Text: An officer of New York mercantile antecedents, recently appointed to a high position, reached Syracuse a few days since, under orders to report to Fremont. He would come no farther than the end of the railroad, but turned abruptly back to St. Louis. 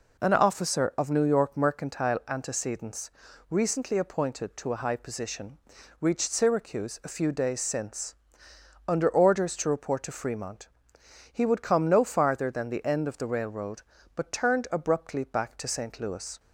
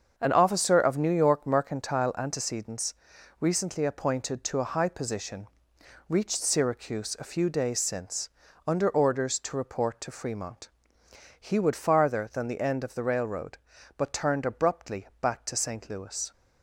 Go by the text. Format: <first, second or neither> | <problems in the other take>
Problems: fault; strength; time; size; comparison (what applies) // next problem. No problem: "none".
first | starts louder than the rest; until 1.1 s; 7 dB // skips "come no"; at 11.7 s